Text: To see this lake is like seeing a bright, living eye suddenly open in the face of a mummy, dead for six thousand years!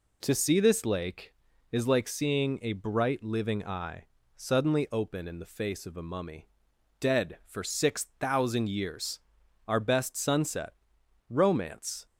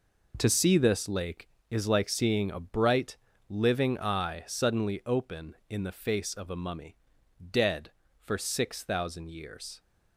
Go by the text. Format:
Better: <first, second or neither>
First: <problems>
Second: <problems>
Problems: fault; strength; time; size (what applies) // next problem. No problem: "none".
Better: second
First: pauses between "eye" and "suddenly"; slight; at 4.0 s; 0.30 s long // goes on to say "Our best sunset romance"; strong; from 9.6 s on; 2.4 s long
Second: none